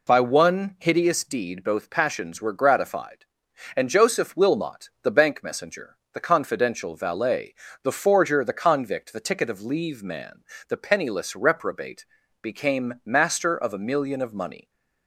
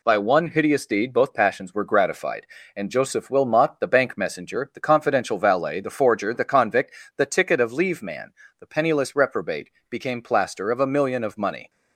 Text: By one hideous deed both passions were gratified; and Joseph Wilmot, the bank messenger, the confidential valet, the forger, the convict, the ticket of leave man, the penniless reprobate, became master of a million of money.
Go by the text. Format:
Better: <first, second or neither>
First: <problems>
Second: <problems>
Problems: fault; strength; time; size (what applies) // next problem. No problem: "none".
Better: first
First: none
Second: says "plaster" for "master"; at 10.1 s